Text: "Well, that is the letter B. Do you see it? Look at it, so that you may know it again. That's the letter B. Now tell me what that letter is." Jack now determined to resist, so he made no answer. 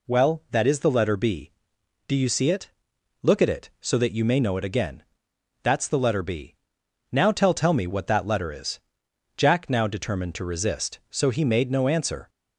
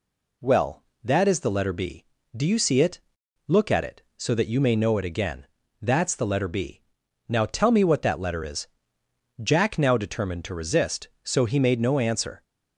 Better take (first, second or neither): second